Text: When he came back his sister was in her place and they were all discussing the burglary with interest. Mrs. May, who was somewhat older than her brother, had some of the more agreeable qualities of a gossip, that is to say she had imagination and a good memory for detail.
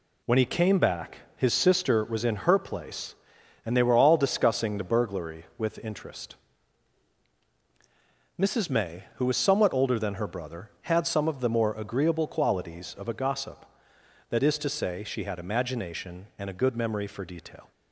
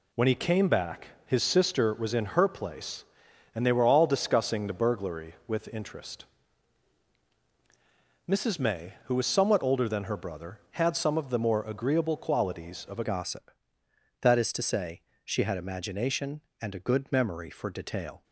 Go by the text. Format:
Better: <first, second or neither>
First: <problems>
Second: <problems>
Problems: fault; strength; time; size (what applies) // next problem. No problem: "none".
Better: first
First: pauses between "back" and "his"; slight; at 1.1 s; 0.18 s long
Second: pauses between "back" and "his"; slight; at 1.0 s; 0.18 s long // changes voice at "gossip"; from 13.0 s on; 5.2 s long // pauses between "say" and "she"; slight; at 15.0 s; 0.24 s long